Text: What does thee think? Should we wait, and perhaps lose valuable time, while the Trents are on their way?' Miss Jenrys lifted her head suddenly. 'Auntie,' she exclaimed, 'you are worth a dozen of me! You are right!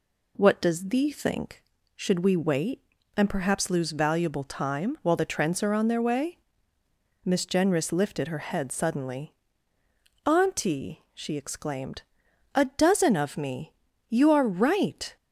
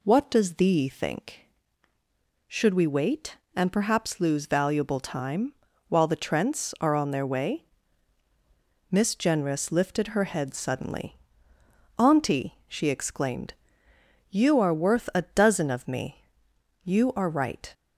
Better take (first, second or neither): second